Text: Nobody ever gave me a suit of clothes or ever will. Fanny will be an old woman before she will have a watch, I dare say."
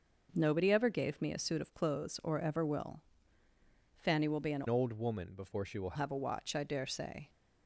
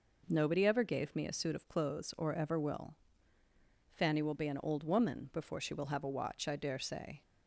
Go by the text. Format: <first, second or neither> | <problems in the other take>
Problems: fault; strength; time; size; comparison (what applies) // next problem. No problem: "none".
second | changes voice from "old" to "will"; from 4.6 to 5.9 s; 1.3 s long